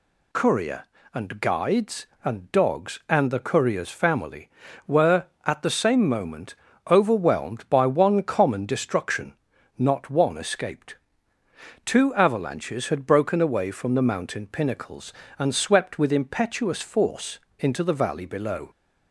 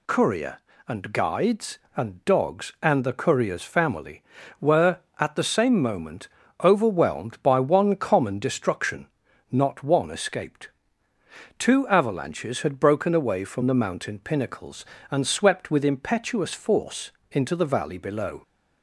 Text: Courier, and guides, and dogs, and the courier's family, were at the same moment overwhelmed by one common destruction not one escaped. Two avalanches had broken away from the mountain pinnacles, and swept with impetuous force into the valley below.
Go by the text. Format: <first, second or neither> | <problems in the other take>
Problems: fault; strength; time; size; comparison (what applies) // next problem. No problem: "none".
neither | pauses between "moment" and "overwhelmed"; slight; the same in both // pauses between "destruction" and "not"; the same in both // pauses between "force" and "into"; slight; the same in both